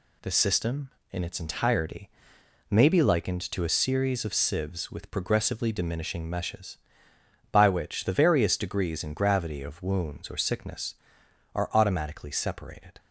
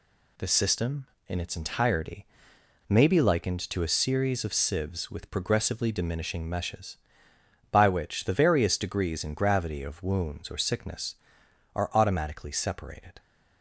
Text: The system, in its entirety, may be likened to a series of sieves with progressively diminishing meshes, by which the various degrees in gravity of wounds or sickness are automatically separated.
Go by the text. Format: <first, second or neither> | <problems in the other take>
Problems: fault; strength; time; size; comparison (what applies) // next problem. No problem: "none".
neither | none